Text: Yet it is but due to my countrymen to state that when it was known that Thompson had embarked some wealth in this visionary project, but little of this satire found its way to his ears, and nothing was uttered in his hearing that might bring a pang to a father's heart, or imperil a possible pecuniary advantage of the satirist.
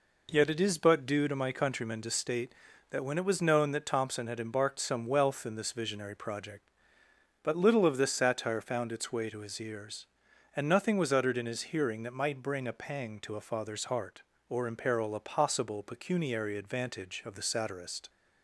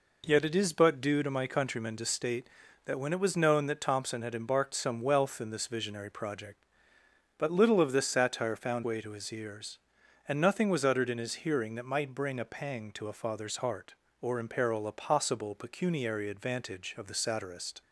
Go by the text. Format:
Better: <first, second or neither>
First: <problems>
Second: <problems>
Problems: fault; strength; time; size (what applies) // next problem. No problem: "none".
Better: first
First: none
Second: skips "its"; at 8.8 s